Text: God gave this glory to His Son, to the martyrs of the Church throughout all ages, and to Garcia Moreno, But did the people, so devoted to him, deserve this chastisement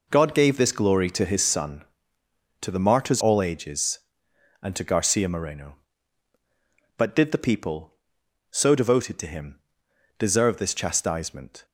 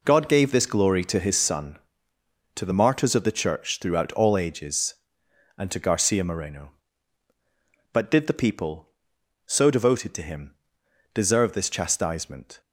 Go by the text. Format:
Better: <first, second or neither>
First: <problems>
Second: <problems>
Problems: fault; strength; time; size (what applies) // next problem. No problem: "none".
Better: second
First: skips "of the Church throughout"; at 3.2 s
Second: none